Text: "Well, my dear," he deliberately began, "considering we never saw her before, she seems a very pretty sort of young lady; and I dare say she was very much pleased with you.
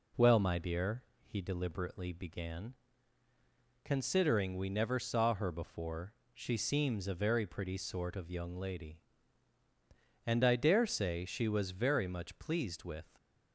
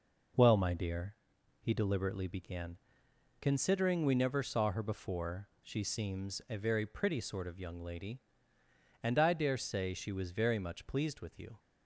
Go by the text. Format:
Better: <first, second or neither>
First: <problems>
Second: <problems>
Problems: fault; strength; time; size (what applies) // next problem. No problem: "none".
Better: second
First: stops before "you"; at 13.1 s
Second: none